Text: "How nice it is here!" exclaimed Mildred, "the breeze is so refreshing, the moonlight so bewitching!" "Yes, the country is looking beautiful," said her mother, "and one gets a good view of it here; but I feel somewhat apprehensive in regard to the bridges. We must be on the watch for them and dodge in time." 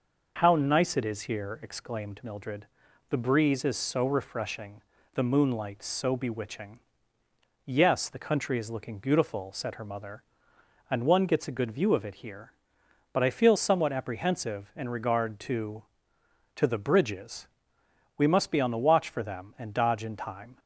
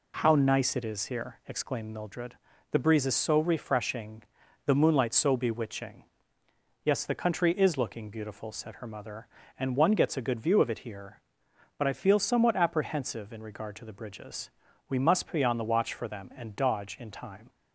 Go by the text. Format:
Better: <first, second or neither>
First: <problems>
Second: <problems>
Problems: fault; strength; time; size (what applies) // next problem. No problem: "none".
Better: second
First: says "to" twice; at 16.5 s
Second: none